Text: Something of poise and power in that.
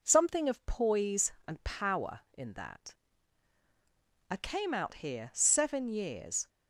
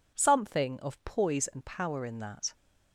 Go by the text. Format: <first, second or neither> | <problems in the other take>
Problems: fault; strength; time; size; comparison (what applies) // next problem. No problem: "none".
second | goes on to say "I came out here seven years"; strong; from 4.3 s on; 2.1 s long